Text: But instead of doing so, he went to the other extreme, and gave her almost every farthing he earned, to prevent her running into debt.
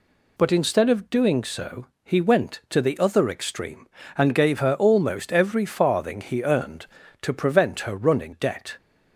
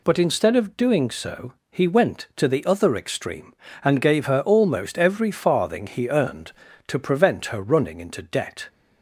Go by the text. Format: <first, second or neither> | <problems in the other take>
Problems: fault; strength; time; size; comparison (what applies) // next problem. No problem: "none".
second | skips "into"; at 8.3 s